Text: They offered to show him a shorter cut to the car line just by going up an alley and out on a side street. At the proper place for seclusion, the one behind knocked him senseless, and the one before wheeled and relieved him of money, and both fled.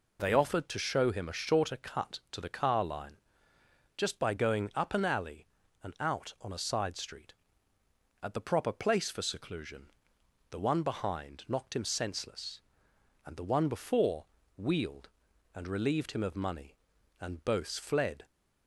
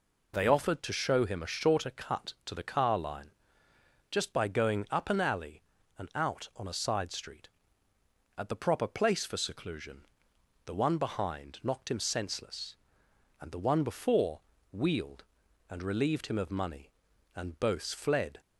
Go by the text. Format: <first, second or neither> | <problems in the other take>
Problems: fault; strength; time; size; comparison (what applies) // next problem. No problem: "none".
neither | pauses between "line" and "just"; noticeable; the same in both // pauses between "before" and "wheeled"; slight; the same in both